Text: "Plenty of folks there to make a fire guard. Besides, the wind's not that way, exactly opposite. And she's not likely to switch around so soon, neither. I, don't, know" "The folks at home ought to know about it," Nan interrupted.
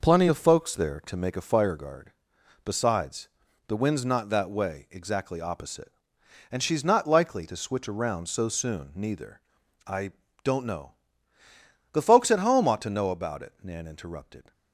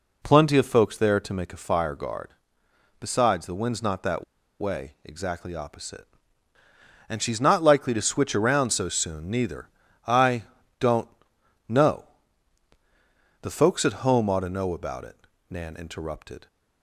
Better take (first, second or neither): first